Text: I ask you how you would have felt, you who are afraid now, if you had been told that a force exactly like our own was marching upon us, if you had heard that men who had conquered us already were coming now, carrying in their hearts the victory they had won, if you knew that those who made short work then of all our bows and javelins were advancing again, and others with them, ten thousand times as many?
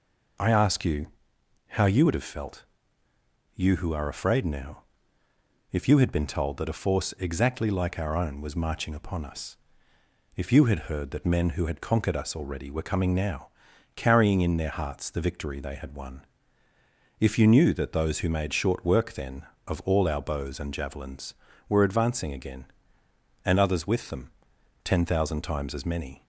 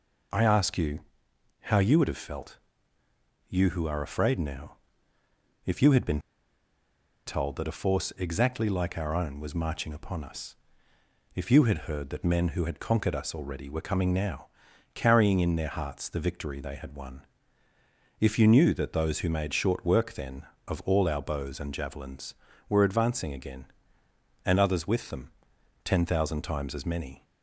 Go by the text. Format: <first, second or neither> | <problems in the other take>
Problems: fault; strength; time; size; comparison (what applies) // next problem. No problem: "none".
first | pauses between "you" and "how"; noticeable; at 0.9 s; 0.62 s long; noticeable in the first // pauses between "been" and "told"; at 6.1 s; 1.0 s long